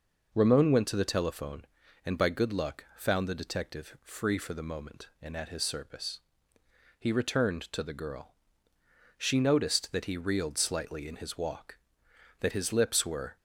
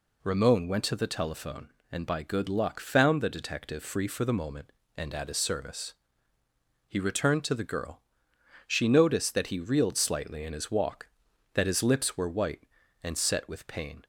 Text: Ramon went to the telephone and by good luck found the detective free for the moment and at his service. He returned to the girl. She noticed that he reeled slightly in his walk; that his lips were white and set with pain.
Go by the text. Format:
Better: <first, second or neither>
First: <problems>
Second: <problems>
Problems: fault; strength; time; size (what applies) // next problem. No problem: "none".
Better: second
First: stops before "white and set with pain"; at 13.3 s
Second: none